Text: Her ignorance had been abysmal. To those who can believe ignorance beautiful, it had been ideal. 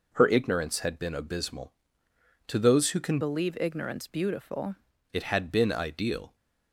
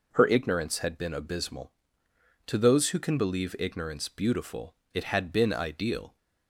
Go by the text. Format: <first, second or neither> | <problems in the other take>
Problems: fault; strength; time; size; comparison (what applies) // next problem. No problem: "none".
second | changes voice from "believe" to "beautiful"; from 3.2 to 4.7 s; 1.5 s long